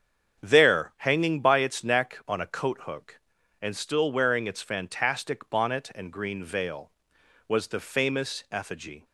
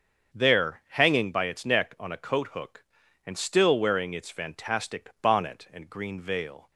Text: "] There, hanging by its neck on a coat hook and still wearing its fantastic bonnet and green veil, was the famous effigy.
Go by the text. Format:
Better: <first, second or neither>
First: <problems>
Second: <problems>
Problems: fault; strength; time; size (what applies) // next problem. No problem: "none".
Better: first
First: starts louder than the rest; strong; until 1.4 s; 7.5 dB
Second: starts louder than the rest; until 1.4 s; 7 dB // stops before "was the famous effigy"; at 6.7 s